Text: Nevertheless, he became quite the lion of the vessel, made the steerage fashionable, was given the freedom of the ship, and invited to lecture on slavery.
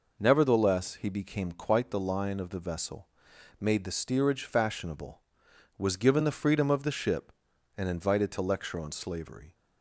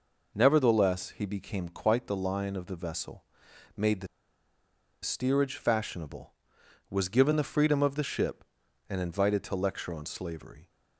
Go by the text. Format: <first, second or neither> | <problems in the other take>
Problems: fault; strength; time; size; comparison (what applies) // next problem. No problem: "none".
first | pauses between "the" and "steerage"; noticeable; at 4.0 s; 0.95 s long